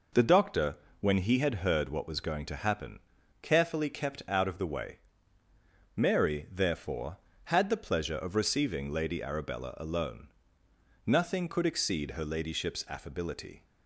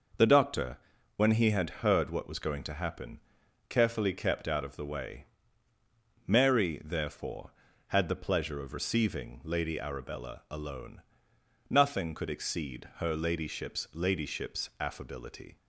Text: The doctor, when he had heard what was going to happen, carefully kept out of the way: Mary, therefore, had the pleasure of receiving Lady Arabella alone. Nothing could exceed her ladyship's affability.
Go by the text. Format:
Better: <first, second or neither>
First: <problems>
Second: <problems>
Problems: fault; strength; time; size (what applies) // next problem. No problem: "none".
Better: first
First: none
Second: says "ladyship's" twice; at 13.9 s